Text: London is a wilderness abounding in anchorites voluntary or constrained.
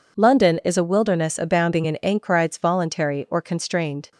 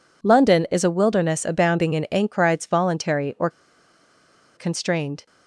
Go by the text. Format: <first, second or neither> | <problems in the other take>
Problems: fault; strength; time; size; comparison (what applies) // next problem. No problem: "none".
first | pauses between "or" and "constrained"; at 3.4 s; 1.0 s long